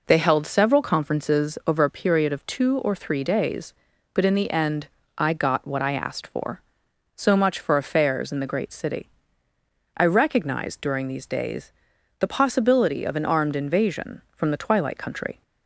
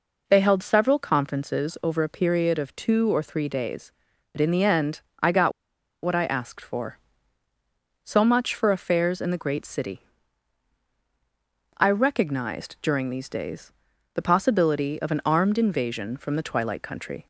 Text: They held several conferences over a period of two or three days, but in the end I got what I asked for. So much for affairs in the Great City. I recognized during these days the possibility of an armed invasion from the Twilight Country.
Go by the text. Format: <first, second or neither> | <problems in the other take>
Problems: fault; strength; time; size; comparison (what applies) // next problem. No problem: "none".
first | pauses between "end" and "I"; slight; at 5.0 s; 0.20 s long; slight in the first // pauses between "got" and "what"; noticeable; at 5.5 s; 0.52 s long // pauses between "days" and "the"; at 13.7 s; 0.42 s long; noticeable in the first